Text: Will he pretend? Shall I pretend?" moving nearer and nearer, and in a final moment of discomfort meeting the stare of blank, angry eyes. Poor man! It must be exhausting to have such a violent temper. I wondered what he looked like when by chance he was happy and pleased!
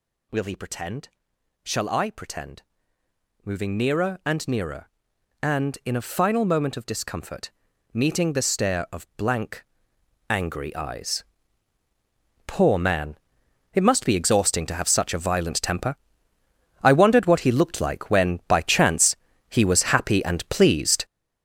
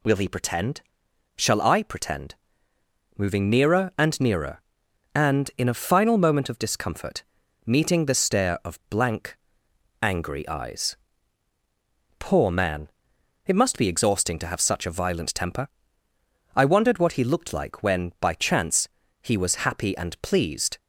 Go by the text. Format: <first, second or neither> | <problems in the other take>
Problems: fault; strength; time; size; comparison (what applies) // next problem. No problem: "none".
second | gets louder; strong; throughout; 9.5 dB // pauses between "discomfort" and "meeting"; at 7.4 s; 0.44 s long; also in the second // pauses between "chance" and "he"; slight; at 19.1 s; 0.34 s long; slight in the second